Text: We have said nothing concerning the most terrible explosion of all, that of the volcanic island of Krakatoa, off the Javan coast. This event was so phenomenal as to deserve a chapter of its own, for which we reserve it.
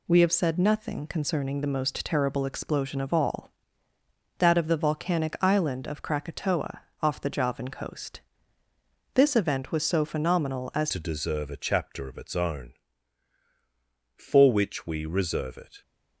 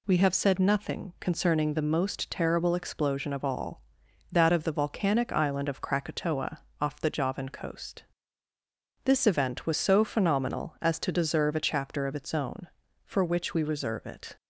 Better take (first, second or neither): second